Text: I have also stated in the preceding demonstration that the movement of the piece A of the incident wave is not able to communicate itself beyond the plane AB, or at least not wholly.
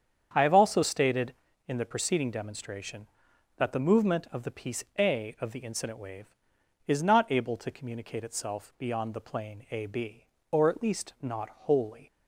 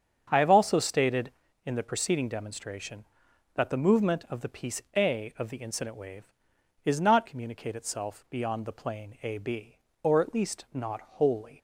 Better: first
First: starts louder than the rest; strong; until 1.3 s; 8 dB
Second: starts louder than the rest; strong; until 1.3 s; 7.5 dB // skips "able to"; at 7.2 s

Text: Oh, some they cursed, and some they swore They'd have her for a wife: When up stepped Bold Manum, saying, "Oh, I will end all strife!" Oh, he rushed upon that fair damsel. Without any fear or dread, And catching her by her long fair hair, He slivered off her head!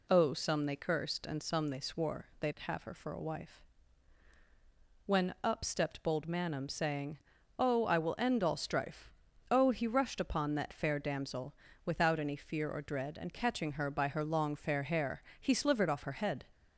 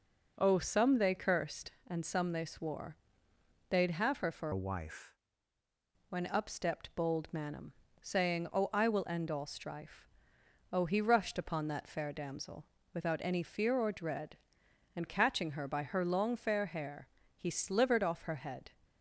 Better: first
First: none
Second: pauses between "swore" and "They'd"; noticeable; at 2.9 s; 0.74 s long // changes voice from "a" to "wife"; from 4.5 to 5.1 s; 0.6 s long

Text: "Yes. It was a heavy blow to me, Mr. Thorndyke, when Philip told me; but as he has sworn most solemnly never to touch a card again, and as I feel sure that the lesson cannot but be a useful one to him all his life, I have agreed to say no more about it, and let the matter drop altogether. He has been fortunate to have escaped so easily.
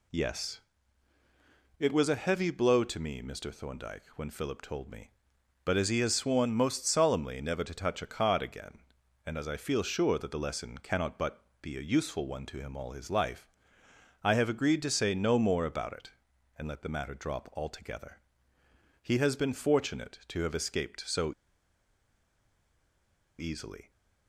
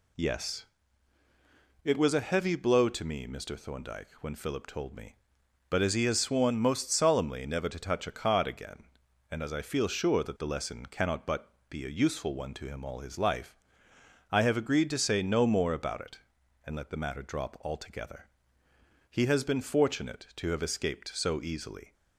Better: second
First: pauses between "but" and "be"; slight; at 11.4 s; 0.18 s long // pauses between "so" and "easily"; strong; at 21.3 s; 2.0 s long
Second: pauses between "but" and "be"; slight; at 11.5 s; 0.18 s long

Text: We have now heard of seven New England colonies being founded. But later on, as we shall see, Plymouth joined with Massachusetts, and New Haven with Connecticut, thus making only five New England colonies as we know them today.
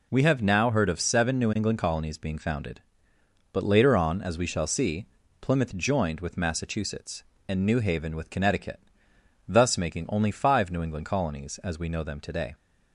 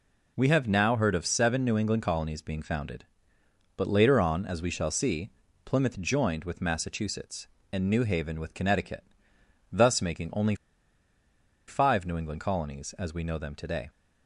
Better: first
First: none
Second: pauses between "only" and "five"; at 10.5 s; 1.1 s long

